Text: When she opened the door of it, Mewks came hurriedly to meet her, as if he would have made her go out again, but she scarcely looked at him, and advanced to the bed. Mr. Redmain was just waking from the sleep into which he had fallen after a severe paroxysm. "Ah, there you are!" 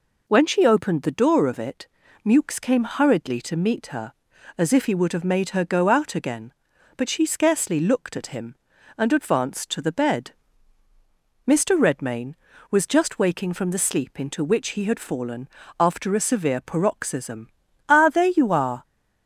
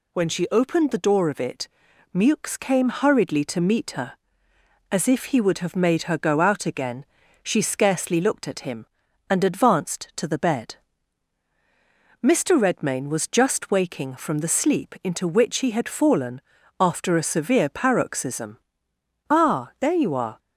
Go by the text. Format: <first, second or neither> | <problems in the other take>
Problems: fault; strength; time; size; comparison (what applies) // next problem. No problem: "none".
first | skips "but"; at 7.2 s // pauses between "fallen" and "after"; at 16.4 s; 0.38 s long; slight in the first